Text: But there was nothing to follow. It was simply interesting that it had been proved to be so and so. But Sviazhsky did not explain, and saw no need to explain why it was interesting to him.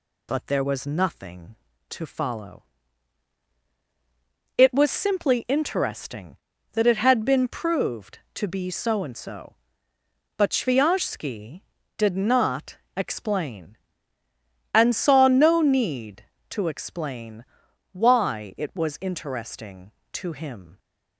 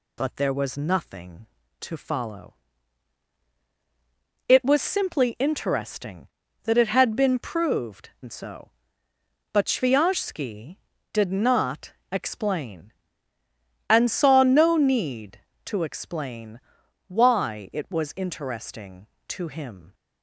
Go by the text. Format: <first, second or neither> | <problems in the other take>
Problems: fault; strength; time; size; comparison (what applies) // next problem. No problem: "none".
first | skips "to be so"; at 8.1 s // pauses between "not" and "explain"; slight; at 11.9 s; 0.18 s long; slight in the first // pauses between "explain" and "why"; noticeable; at 16.5 s; 0.52 s long; noticeable in the first